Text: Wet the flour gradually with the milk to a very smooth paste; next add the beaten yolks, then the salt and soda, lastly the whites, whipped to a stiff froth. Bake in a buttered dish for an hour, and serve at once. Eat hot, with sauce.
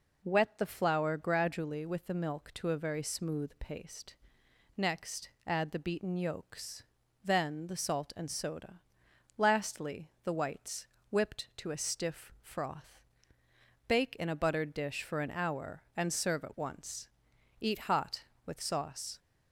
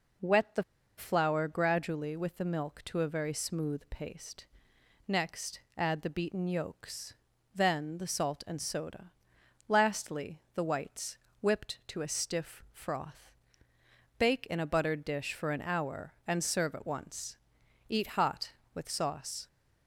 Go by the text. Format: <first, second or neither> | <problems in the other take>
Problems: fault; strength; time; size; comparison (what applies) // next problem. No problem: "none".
first | pauses between "the" and "flour"; slight; at 0.6 s; 0.34 s long // pauses between "next" and "add"; slight; at 5.6 s; 0.16 s long; slight in the first